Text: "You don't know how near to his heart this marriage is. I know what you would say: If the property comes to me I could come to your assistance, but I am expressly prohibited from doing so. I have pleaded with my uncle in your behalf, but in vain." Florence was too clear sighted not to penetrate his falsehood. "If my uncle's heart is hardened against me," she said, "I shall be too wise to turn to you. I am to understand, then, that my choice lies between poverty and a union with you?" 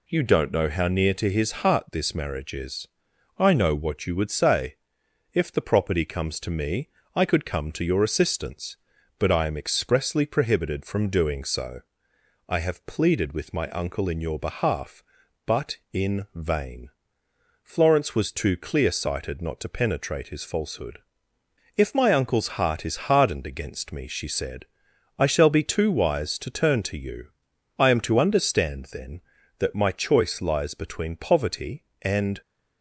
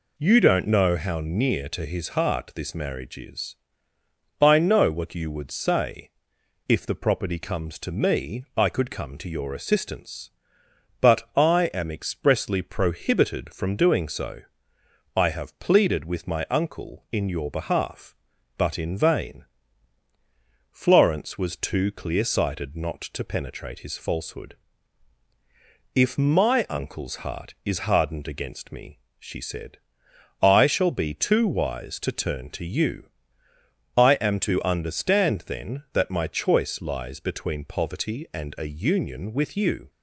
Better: second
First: pauses between "me" and "I"; slight; at 6.8 s; 0.26 s long // stops before "a union with you"; at 32.4 s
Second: none

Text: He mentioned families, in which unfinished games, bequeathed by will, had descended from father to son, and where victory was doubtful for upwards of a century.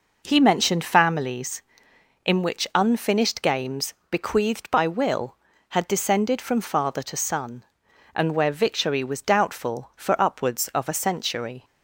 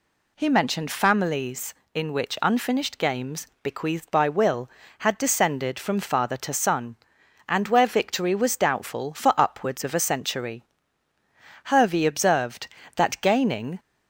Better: first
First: none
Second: goes on to say "Hervey observed that gaining"; strong; from 11.6 s on; 2.1 s long

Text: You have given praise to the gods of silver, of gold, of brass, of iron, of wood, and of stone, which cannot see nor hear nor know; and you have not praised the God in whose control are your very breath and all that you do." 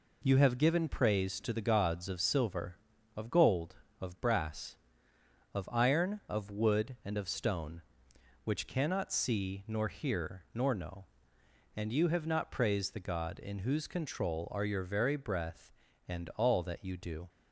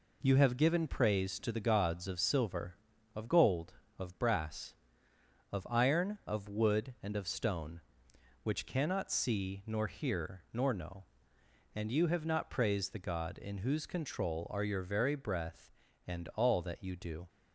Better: neither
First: none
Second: none

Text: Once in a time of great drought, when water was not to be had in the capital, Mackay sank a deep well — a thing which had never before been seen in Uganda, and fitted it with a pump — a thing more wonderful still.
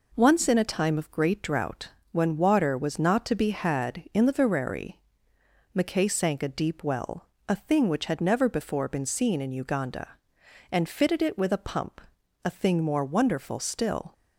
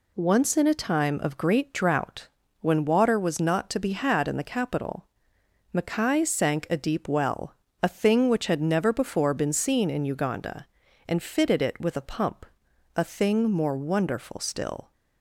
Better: second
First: says "vereri" for "capital"; at 4.3 s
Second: none

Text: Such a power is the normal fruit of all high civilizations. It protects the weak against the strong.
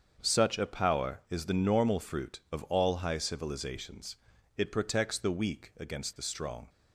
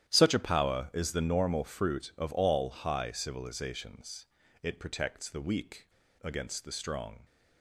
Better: first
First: starts louder than the rest; until 1.2 s; 7 dB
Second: starts louder than the rest; strong; until 1.1 s; 11 dB // pauses between "weak" and "against"; slight; at 5.8 s; 0.35 s long

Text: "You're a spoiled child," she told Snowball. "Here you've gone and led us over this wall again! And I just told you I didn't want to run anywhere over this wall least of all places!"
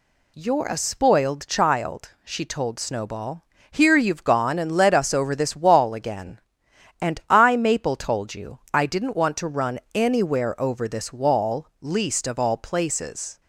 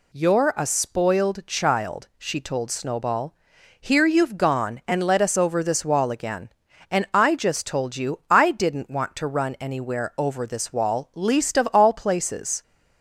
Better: second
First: says "maple" for "just"; at 7.5 s // pauses between "run" and "anywhere"; slight; at 9.7 s; 0.16 s long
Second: none

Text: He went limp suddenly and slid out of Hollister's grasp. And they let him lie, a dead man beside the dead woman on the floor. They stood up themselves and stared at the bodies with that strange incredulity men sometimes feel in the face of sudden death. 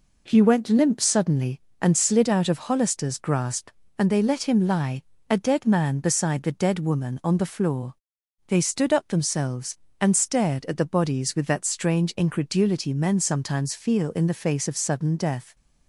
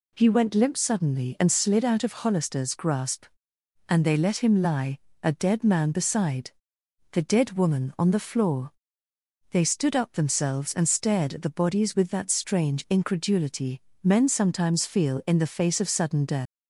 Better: first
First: none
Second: pauses between "beside" and "the"; noticeable; at 6.5 s; 0.62 s long // pauses between "incredulity" and "men"; slight; at 13.8 s; 0.18 s long // leaves "death" unfinished; at 16.4 s; 180 ms

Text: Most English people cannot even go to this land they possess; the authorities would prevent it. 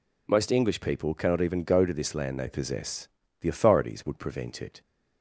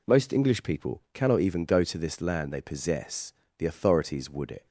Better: first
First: none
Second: skips "prevent"; at 4.5 s

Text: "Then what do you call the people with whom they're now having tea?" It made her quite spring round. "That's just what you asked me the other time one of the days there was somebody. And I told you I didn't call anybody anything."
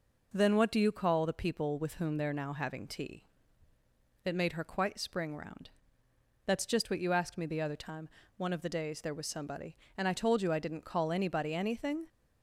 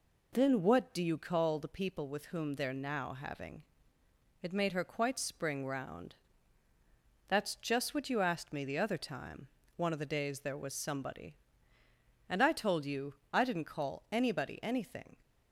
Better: first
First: pauses between "time" and "one"; slight; at 8.0 s; 0.30 s long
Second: skips "tea"; at 4.0 s // pauses between "time" and "one"; slight; at 9.4 s; 0.30 s long // pauses between "you" and "I"; slight; at 13.1 s; 0.18 s long

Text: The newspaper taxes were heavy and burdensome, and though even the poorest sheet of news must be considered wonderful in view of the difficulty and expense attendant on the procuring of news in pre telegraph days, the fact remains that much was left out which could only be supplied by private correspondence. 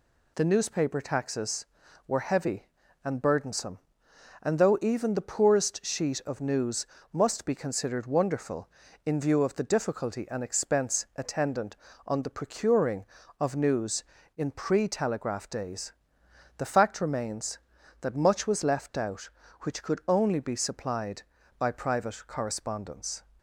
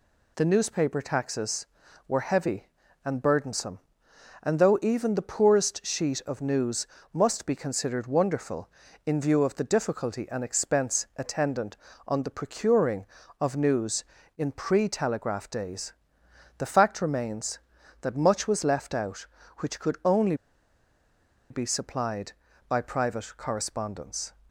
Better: first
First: pauses between "news" and "must"; slight; at 6.8 s; 0.24 s long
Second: pauses between "news" and "must"; slight; at 6.8 s; 0.24 s long // pauses between "only" and "be"; at 20.3 s; 1.1 s long

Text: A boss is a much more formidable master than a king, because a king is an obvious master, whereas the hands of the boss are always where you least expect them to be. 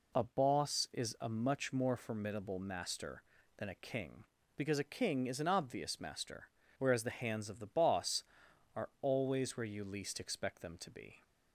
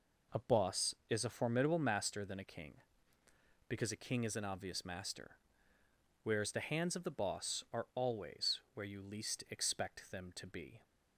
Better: first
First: none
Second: skips "much more"; at 1.3 s

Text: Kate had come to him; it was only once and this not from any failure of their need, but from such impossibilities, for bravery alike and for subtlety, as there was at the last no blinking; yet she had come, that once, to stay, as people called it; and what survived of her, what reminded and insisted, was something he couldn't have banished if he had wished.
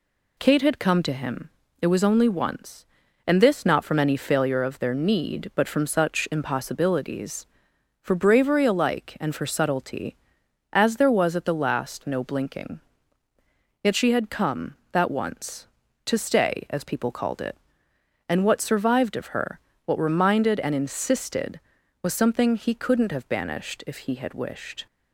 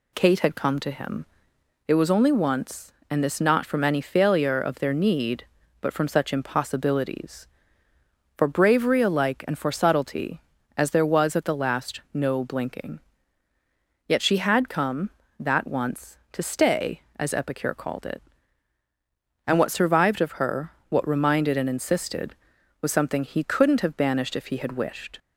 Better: first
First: none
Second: says "epicure" for "people"; at 17.3 s

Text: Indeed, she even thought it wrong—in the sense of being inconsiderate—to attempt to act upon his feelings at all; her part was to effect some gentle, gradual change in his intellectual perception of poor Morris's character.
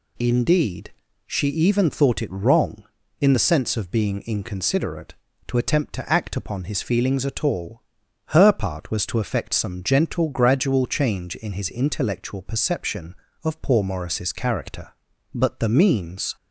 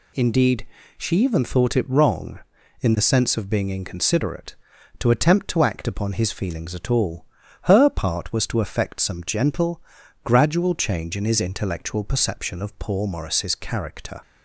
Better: second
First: goes on to say "But the means"; noticeable; from 15.3 s on; 1.0 s long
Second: none

